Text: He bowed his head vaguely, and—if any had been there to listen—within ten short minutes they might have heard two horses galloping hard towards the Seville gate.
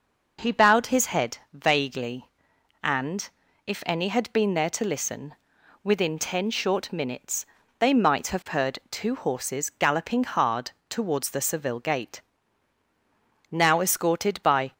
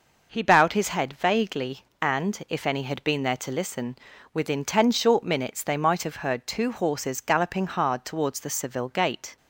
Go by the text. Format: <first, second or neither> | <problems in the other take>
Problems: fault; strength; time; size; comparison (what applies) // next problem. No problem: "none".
second | pauses between "head" and "vaguely"; slight; at 1.3 s; 0.16 s long // pauses between "minutes" and "they"; slight; at 7.4 s; 0.34 s long // pauses between "hard" and "towards"; slight; at 10.7 s; 0.16 s long // goes on to say "Now escorted by"; noticeable; from 13.5 s on; 1.2 s long